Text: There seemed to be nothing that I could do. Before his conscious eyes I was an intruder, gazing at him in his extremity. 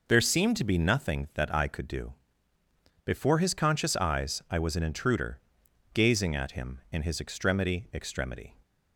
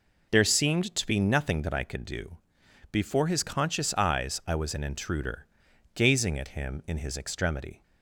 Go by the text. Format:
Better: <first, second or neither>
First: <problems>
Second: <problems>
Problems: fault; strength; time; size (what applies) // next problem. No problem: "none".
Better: second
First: says "extremity" twice; at 7.9 s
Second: none